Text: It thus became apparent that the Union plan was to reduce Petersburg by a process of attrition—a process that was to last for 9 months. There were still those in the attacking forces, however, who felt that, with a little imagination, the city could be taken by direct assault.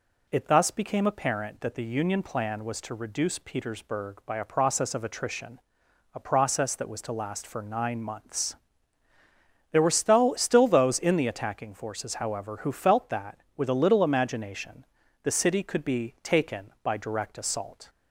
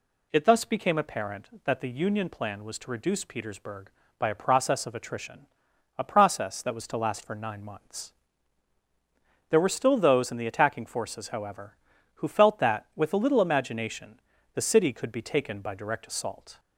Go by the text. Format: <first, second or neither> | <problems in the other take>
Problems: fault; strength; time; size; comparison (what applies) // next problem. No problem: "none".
second | says "still" twice; at 10.3 s